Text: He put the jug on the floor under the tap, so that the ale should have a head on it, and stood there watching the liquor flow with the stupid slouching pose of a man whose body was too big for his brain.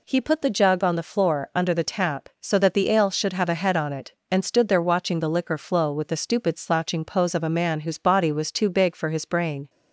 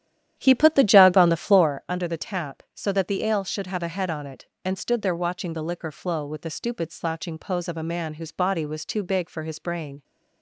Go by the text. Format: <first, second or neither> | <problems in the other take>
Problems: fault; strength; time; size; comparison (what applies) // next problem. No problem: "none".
first | starts louder than the rest; strong; until 1.8 s; 11 dB